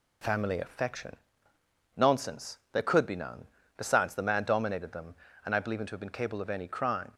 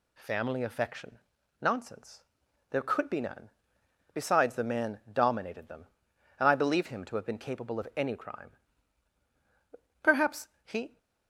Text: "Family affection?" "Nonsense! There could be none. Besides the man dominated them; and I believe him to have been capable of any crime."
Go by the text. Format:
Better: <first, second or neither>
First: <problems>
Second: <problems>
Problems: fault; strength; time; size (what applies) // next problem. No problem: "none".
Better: first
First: none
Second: goes on to say "Perhaps he"; noticeable; from 10.0 s on; 0.96 s long